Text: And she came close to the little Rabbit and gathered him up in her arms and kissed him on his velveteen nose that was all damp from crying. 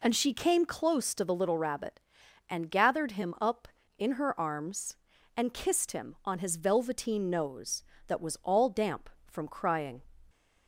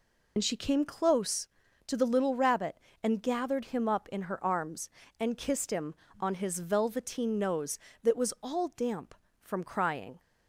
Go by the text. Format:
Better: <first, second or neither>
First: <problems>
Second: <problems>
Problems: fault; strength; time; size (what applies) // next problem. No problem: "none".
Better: first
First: none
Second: loses the start of "And"; at 0.3 s; 40 ms